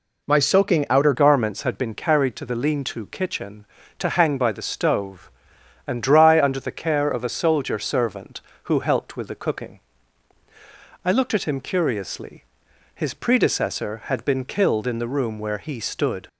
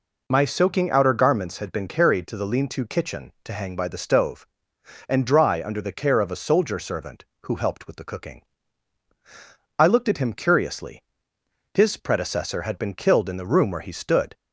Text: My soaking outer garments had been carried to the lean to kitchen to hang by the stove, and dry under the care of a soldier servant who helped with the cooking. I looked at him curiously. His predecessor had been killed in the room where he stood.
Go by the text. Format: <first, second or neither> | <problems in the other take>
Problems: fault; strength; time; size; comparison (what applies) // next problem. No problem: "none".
second | changes voice at "garments"; from 1.1 s on; 15.1 s long